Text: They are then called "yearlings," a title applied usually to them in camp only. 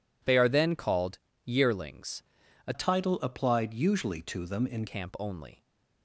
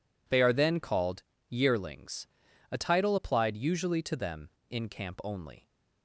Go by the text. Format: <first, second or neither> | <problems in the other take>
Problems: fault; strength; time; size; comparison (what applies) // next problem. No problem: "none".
second | pauses between "called" and "yearlings"; slight; at 1.1 s; 0.26 s long; slight in the second // changes voice from "title" to "in"; from 2.7 to 4.8 s; 2.1 s long